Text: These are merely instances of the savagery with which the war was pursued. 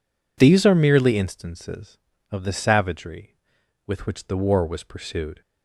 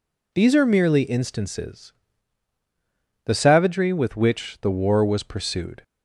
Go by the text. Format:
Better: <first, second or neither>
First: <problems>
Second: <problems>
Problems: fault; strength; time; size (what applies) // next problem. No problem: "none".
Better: first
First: none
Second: skips "of"; at 2.5 s